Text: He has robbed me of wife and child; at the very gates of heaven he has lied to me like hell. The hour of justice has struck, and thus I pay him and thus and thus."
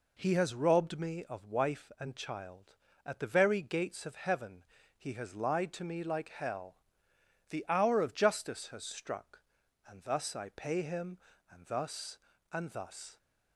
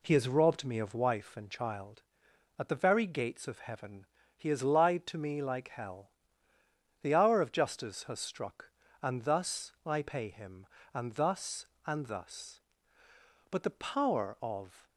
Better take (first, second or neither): first